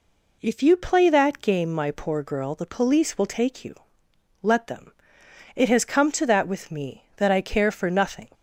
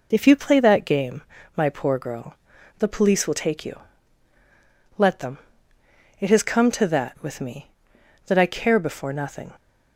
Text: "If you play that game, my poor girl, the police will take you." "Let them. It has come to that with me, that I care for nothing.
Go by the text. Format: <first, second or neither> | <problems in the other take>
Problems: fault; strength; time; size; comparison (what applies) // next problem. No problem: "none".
first | says "before" for "for"; at 8.7 s